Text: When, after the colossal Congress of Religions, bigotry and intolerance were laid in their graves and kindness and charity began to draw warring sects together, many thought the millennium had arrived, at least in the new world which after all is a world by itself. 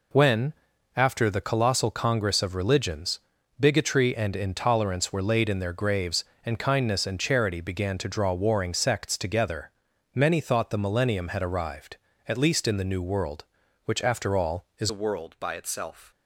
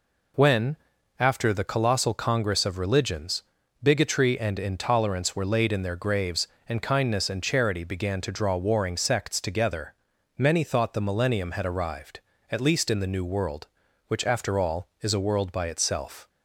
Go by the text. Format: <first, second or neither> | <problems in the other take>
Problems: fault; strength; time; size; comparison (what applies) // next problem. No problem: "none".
second | changes voice at "a"; from 14.8 s on; 1.3 s long